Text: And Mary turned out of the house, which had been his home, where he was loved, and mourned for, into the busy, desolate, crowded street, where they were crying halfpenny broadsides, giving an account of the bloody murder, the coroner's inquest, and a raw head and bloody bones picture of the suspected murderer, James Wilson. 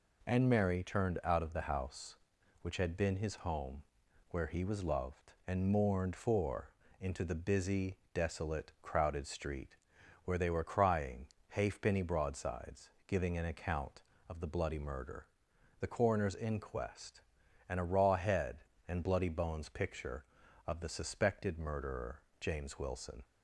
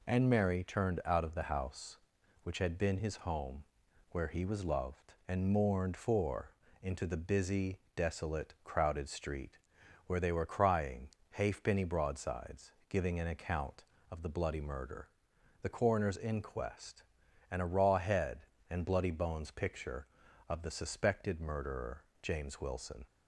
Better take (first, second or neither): neither